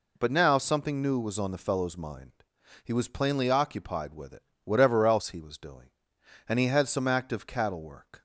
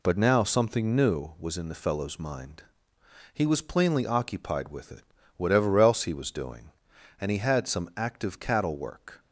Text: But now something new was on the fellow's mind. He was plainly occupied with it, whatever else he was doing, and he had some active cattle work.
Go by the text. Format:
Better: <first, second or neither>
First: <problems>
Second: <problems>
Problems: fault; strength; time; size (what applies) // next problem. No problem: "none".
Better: first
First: none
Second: says "in" for "on"; at 1.5 s